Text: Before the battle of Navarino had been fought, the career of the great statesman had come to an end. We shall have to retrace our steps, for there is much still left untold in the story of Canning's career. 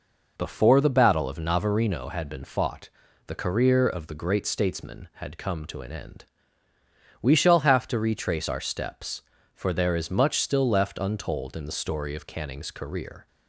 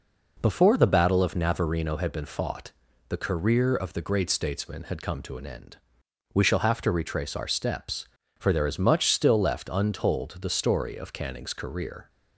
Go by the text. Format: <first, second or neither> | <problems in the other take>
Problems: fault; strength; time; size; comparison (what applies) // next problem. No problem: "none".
first | skips "in"; at 10.3 s